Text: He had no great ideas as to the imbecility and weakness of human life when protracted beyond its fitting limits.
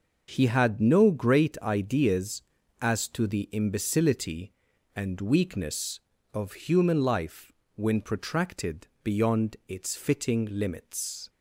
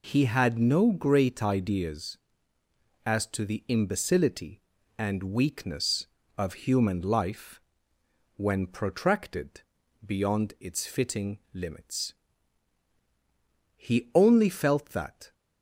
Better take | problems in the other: first | pauses between "life" and "when"; noticeable; at 7.6 s; 0.74 s long; slight in the first // pauses between "protracted" and "beyond"; at 9.6 s; 0.44 s long; slight in the first // goes on to say "He only felt that"; from 13.7 s on; 1.5 s long

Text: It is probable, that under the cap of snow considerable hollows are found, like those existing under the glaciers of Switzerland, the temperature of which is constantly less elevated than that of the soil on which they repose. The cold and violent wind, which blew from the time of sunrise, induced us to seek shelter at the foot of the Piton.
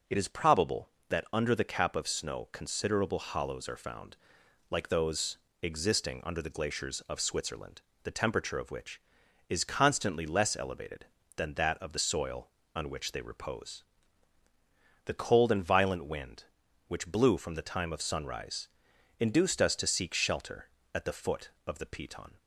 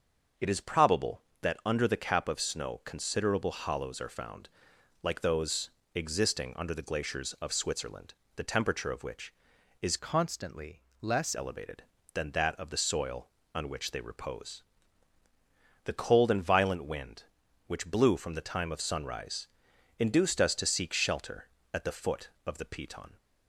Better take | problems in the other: first | starts louder than the rest; noticeable; until 1.5 s; 6 dB // pauses between "those" and "existing"; slight; at 5.7 s; 0.24 s long; slight in the first // changes voice from "constantly" to "less"; from 9.9 to 11.3 s; 1.4 s long // pauses between "constantly" and "less"; slight; at 10.8 s; 0.18 s long

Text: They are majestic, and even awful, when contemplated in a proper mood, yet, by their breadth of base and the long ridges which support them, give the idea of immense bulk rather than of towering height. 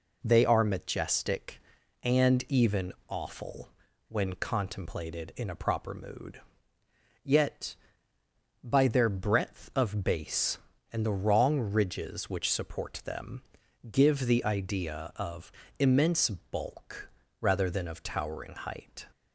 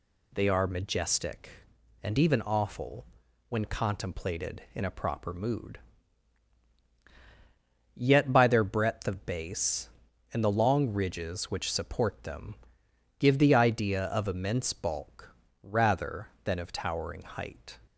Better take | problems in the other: second | pauses between "even" and "awful"; slight; at 2.9 s; 0.16 s long // says "wrong" for "long"; at 11.1 s // pauses between "of" and "immense"; slight; at 15.5 s; 0.28 s long // pauses between "bulk" and "rather"; slight; at 17.0 s; 0.30 s long; slight in the second

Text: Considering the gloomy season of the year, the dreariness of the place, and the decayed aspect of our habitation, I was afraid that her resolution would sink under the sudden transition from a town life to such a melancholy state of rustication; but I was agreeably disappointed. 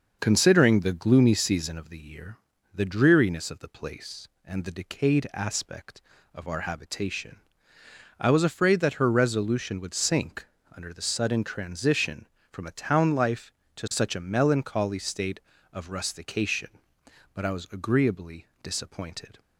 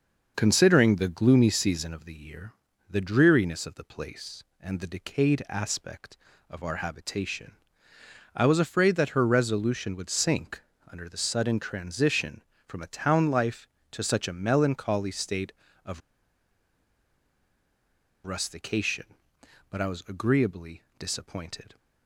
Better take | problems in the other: first | starts louder than the rest; until 1.3 s; 6.5 dB; also in the first // pauses between "sink" and "under"; slight; at 10.6 s; 0.30 s long; slight in the first // pauses between "of" and "rustication"; strong; at 16.0 s; 2.2 s long // pauses between "agreeably" and "disappointed"; slight; at 20.8 s; 0.16 s long; slight in the first

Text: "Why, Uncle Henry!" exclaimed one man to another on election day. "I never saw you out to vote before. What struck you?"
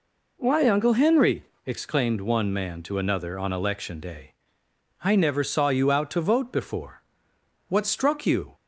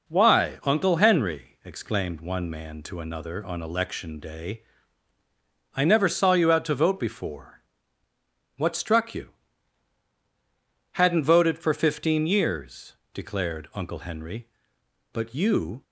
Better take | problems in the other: first | goes on to say "Hadn't voted for fifteen years declared Uncle Henry but you"; strong; from 10.9 s on; 4.9 s long

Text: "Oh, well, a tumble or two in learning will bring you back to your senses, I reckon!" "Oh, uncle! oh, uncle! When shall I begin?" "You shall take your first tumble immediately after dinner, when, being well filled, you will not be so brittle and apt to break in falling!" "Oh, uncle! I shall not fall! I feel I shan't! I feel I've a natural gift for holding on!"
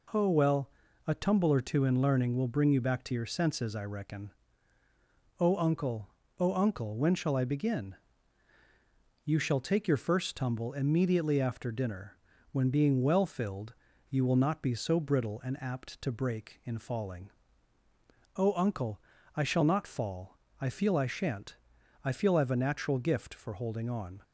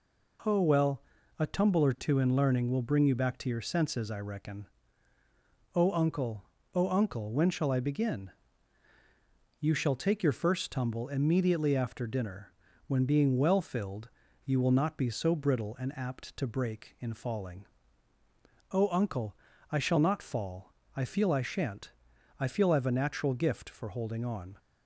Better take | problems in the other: neither | none

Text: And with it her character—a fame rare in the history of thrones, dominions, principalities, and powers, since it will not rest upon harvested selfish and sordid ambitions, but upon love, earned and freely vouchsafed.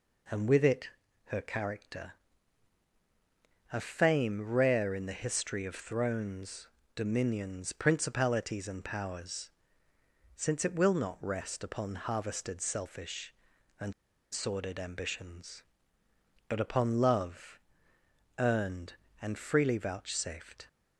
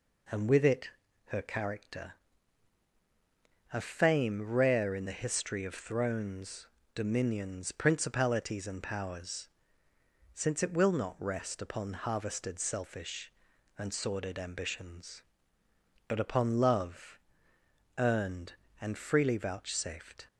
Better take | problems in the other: second | pauses between "it" and "her"; at 0.8 s; 0.38 s long; also in the second // pauses between "and" and "sordid"; at 13.9 s; 0.40 s long

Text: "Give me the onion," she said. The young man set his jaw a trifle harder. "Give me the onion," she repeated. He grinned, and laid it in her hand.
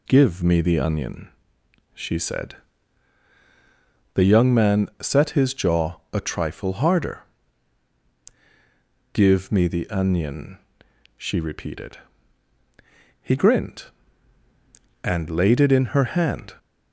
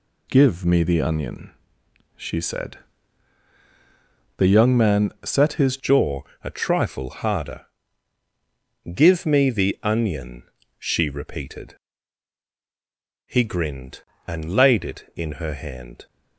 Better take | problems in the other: first | changes voice at "jaw"; from 5.7 s on; 10.3 s long // pauses between "jaw" and "a"; slight; at 6.2 s; 0.20 s long

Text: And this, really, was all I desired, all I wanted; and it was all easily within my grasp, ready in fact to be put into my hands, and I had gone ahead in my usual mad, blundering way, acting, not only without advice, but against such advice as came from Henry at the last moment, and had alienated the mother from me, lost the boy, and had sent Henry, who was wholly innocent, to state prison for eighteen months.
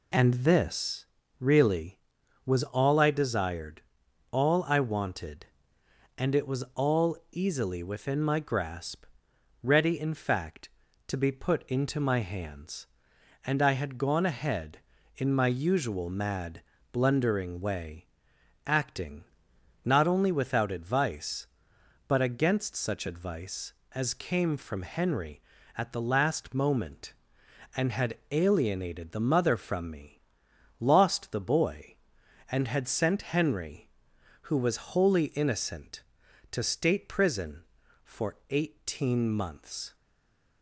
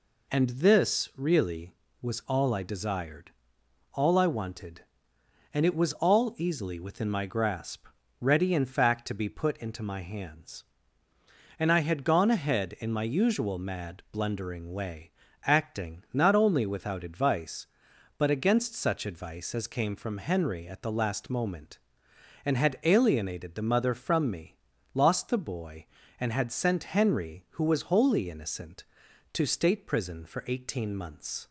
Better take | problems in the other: second | stays silent after the last word; slight; from 39.9 s on; 0.7 s long

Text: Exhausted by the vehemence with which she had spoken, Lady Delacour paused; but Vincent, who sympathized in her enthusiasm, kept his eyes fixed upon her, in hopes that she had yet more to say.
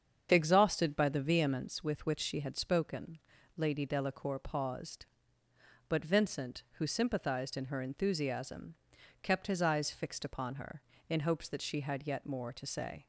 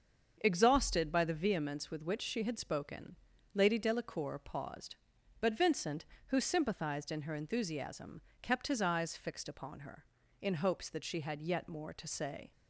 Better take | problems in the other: neither | starts louder than the rest; the same in both

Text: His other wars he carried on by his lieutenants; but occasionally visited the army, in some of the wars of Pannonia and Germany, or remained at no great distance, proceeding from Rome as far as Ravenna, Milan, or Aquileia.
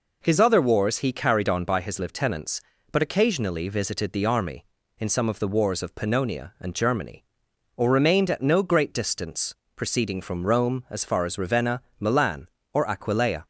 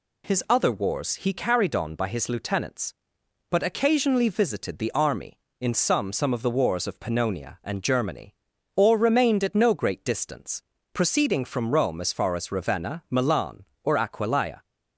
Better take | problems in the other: first | says "some" twice; at 6.1 s

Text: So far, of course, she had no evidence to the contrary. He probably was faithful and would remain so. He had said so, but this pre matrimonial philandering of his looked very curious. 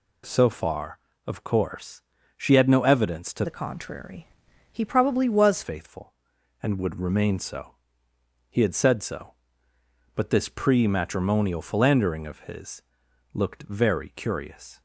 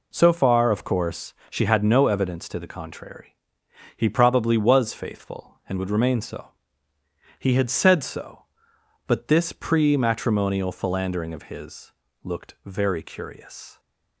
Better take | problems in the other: second | changes voice from "the" to "was"; from 3.4 to 5.6 s; 2.2 s long // pauses between "his" and "looked"; noticeable; at 12.8 s; 0.52 s long; slight in the second

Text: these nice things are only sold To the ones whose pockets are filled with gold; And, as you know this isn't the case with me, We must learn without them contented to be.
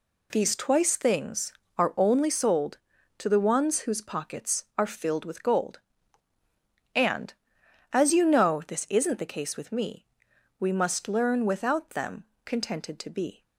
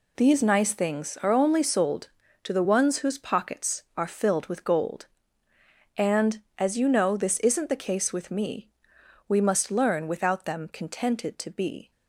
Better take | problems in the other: second | says "twice" for "nice"; at 0.5 s // pauses between "them" and "contented"; slight; at 12.2 s; 0.20 s long

